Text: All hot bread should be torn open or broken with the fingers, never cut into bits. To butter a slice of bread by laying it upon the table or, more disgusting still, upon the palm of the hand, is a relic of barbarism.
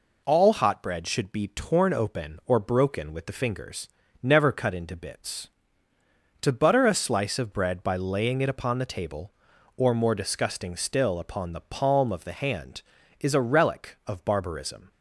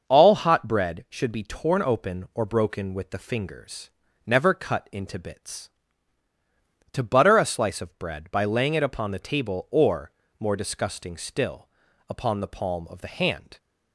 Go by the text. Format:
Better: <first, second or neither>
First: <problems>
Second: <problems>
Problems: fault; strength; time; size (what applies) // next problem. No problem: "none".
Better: first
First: none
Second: starts louder than the rest; until 1.1 s; 6 dB // stops before "is a relic of barbarism"; at 13.5 s